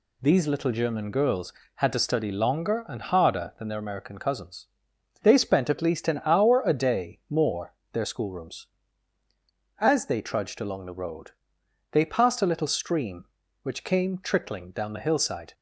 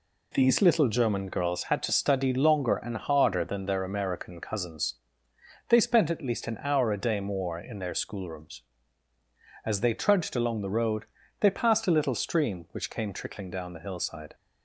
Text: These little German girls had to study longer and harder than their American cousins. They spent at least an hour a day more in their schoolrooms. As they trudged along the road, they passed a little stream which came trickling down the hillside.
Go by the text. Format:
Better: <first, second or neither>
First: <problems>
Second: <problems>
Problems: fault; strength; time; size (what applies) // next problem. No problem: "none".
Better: second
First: skips "in"; at 7.8 s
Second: none